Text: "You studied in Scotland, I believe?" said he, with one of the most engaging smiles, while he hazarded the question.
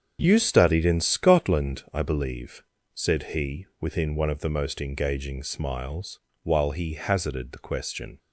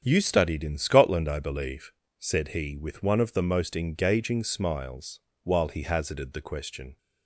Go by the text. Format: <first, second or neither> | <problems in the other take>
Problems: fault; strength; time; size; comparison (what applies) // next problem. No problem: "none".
second | starts louder than the rest; strong; until 1.2 s; 7.5 dB; strong in the second // says "within" for "with"; at 3.8 s